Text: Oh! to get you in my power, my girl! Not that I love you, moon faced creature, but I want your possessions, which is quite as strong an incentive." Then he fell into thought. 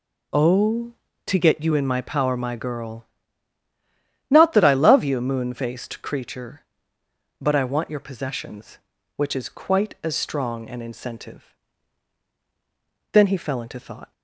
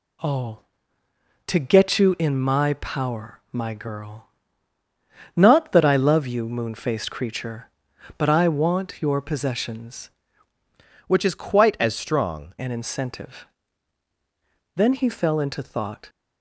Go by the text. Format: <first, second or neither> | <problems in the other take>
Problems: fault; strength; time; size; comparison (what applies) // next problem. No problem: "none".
first | changes voice from "which" to "strong"; from 11.0 to 12.5 s; 1.5 s long